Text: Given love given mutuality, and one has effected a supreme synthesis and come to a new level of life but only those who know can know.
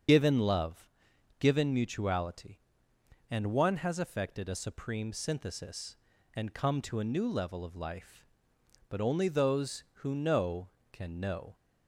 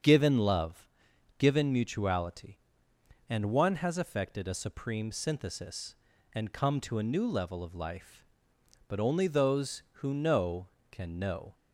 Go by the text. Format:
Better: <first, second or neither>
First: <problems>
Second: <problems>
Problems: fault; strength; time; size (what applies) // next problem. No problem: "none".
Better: second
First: loses the start of "Given"; at 0.0 s; 40 ms // starts louder than the rest; until 1.5 s; 7 dB // pauses between "love" and "given"; noticeable; at 0.8 s; 0.50 s long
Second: starts louder than the rest; until 1.5 s; 7 dB // pauses between "love" and "given"; noticeable; at 0.8 s; 0.50 s long